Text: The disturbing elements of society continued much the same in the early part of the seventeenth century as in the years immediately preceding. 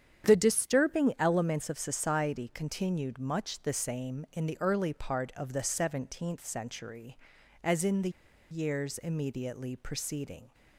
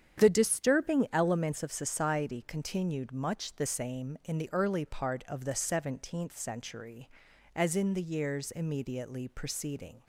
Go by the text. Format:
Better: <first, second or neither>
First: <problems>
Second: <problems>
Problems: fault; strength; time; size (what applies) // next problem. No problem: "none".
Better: second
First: starts louder than the rest; strong; until 1.3 s; 8.5 dB // pauses between "the" and "years"; at 8.0 s; 0.41 s long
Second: starts louder than the rest; strong; until 1.2 s; 9 dB